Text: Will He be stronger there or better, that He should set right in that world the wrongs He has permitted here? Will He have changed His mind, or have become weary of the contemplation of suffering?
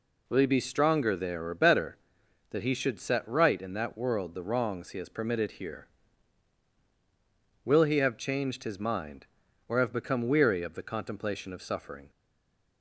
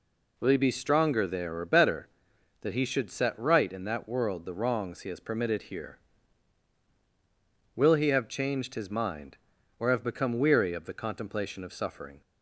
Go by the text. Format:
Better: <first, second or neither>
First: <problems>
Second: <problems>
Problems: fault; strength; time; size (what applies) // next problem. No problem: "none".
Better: second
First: stays silent after the last word; slight; from 12.0 s on; 0.8 s long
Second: none